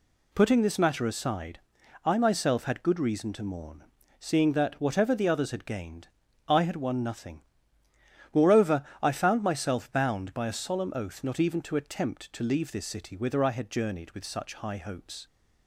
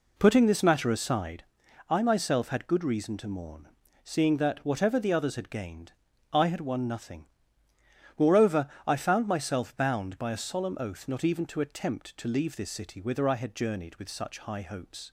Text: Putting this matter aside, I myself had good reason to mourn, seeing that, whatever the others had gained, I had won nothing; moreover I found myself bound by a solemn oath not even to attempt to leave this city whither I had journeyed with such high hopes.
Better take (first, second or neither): first